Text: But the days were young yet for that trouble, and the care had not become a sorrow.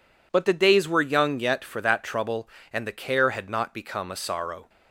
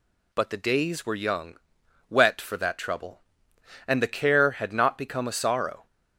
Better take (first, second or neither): first